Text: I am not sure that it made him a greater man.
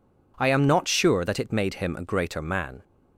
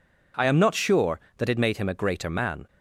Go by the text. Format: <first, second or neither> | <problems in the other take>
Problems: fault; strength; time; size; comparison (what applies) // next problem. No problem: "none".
neither | none